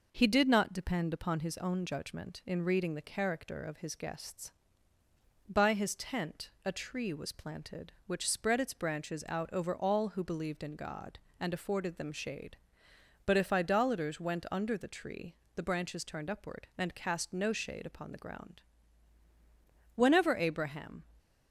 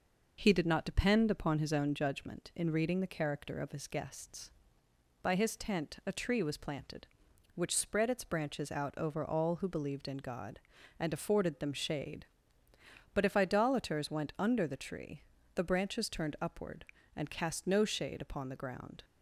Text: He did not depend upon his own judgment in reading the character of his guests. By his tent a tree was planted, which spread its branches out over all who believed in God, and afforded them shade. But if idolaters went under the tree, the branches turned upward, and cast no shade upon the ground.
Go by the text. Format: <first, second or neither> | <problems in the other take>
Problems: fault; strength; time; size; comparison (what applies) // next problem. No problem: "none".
second | goes on to say "Whenever Abraham"; noticeable; from 19.9 s on; 1.1 s long